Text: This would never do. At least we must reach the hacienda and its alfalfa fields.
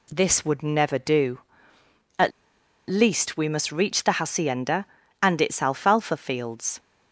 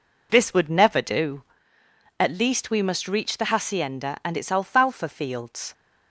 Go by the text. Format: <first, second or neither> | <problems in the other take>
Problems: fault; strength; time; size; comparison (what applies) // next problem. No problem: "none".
second | pauses between "At" and "least"; noticeable; at 2.3 s; 0.58 s long